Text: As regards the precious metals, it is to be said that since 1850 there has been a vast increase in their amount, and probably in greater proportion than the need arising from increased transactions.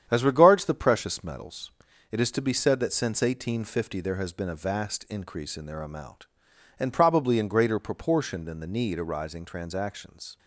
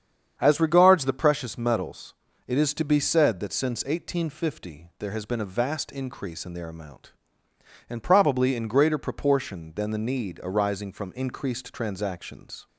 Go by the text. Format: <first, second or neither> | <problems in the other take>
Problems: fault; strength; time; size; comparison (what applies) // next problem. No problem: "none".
second | starts louder than the rest; strong; until 1.1 s; 9 dB; strong in the second // skips "from increased"; at 9.4 s